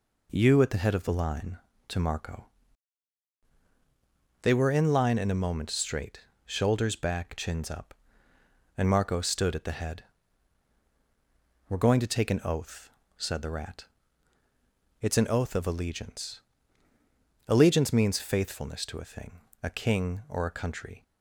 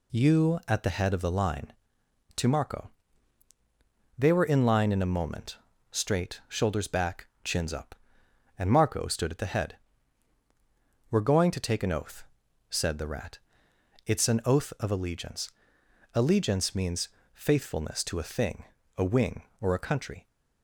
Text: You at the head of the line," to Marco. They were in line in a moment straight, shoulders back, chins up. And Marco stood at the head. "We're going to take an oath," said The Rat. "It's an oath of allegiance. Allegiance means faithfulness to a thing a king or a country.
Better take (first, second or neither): first